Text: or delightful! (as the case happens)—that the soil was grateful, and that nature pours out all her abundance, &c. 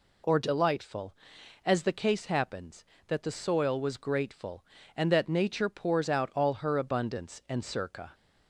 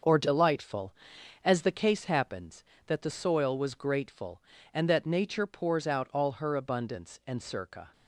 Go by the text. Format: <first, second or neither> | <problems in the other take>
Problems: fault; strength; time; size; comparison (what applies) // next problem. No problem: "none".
first | gets quieter; strong; throughout; 8 dB